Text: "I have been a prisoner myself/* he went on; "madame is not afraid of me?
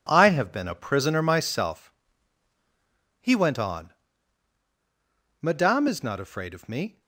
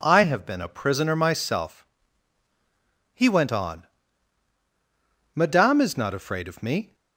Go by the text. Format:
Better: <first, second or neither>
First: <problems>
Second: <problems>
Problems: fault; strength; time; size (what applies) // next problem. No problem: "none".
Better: second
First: gets quieter; strong; throughout; 10.5 dB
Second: none